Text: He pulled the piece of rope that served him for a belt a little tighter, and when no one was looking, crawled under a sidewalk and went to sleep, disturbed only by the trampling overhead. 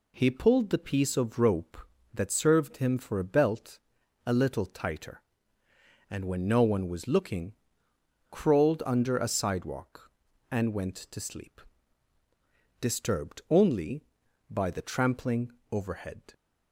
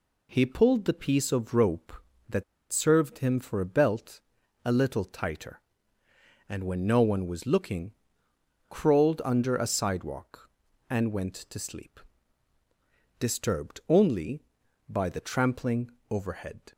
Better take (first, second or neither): first